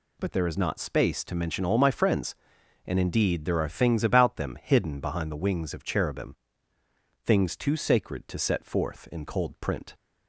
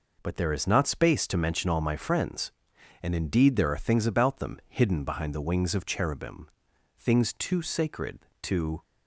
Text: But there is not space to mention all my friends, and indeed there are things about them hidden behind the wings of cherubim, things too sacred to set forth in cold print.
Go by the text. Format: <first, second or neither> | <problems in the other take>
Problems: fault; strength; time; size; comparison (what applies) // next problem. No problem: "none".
first | stops before "set forth in cold print"; at 8.8 s